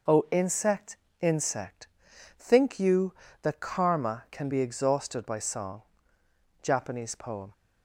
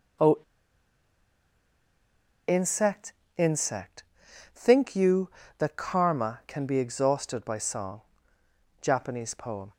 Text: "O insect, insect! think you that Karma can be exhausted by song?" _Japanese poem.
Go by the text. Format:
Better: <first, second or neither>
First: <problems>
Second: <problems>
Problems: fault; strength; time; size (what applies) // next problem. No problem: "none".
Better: first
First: none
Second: pauses between "O" and "insect"; strong; at 0.3 s; 2.0 s long